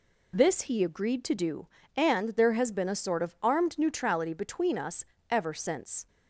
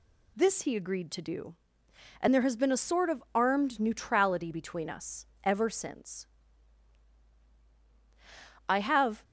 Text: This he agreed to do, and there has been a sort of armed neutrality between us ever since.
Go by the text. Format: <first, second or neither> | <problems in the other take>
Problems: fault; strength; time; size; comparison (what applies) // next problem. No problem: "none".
first | pauses between "us" and "ever"; slight; at 5.2 s; 0.16 s long; slight in the first // goes on to say "I have"; from 8.6 s on; 0.56 s long